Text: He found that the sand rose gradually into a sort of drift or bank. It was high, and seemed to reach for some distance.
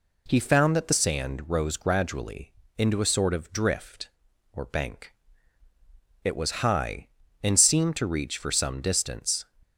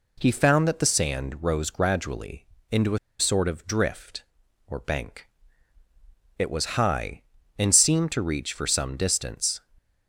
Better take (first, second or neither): first